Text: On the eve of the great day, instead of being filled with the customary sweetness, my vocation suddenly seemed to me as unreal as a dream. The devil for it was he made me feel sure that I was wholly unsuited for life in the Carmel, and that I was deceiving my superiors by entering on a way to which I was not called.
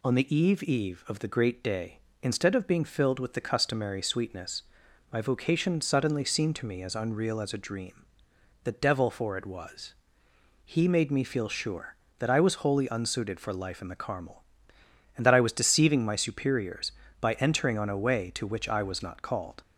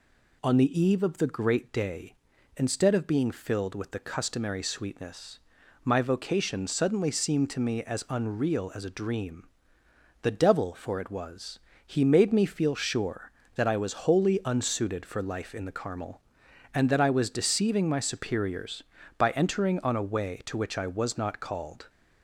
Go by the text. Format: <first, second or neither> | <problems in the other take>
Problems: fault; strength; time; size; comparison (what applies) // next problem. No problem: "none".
second | says "eve" twice; at 0.6 s // pauses between "was" and "he"; noticeable; at 9.9 s; 0.72 s long; slight in the second